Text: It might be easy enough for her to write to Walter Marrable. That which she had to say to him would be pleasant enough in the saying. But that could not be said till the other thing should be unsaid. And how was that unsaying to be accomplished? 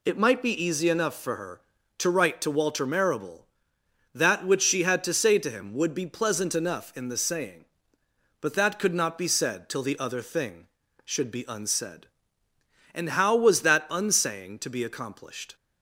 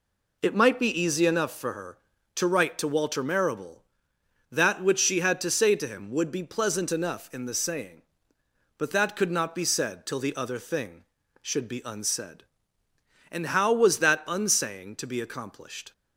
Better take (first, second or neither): first